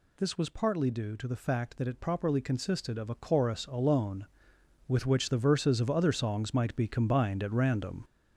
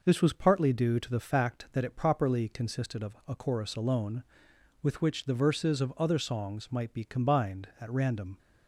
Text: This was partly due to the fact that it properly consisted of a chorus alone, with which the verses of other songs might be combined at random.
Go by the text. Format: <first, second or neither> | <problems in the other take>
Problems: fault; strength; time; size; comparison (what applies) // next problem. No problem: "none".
second | gets louder; throughout; 6 dB